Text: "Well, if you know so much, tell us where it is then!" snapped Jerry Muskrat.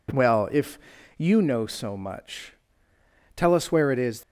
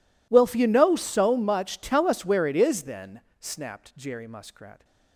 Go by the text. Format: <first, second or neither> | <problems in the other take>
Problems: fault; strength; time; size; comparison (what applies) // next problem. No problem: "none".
second | pauses between "if" and "you"; at 0.7 s; 0.38 s long // stops before "then snapped Jerry Muskrat"; at 4.2 s